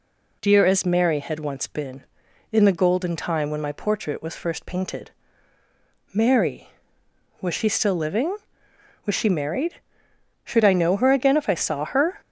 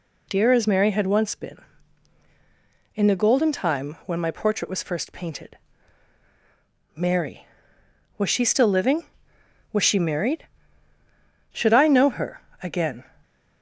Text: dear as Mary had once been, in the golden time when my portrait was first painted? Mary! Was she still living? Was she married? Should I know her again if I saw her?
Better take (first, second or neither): first